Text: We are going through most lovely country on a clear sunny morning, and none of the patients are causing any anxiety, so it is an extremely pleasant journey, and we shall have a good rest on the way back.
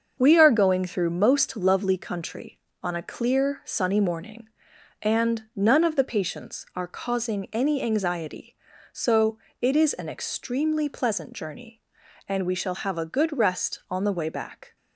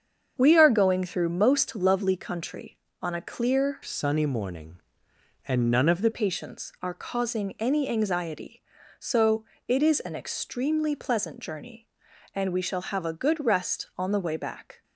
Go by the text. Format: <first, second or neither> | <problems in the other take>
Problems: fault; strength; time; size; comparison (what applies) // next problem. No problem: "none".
first | starts louder than the rest; strong; until 1.3 s; 7 dB; also in the first // changes voice from "sunny" to "the"; from 3.8 to 6.1 s; 2.3 s long // pauses between "so" and "it"; slight; at 9.4 s; 0.24 s long; slight in the first